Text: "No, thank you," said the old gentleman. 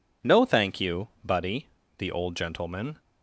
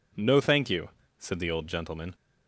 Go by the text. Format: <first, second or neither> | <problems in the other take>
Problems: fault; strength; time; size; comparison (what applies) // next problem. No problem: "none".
second | says "buddy" for "said"; at 1.2 s